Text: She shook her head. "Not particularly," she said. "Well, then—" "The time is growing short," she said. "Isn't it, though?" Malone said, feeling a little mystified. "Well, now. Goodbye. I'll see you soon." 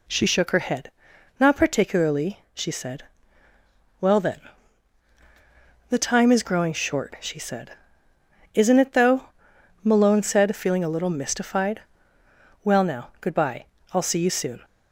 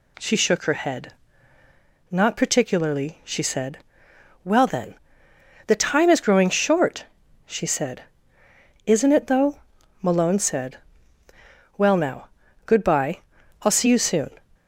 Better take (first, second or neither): first